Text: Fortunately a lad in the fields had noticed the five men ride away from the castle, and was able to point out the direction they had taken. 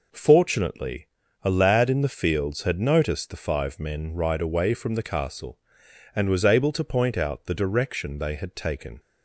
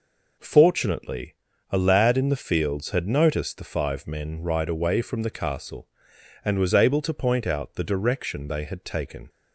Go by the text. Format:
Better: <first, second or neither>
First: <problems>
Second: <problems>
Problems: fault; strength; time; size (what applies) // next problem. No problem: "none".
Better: neither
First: pauses between "Fortunately" and "a"; at 1.0 s; 0.38 s long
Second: pauses between "Fortunately" and "a"; at 1.3 s; 0.38 s long